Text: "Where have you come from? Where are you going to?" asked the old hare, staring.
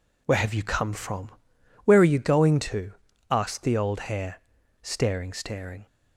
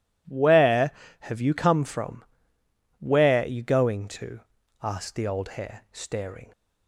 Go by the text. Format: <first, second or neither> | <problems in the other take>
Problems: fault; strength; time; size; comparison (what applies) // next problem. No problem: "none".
second | says "staring" twice; at 5.3 s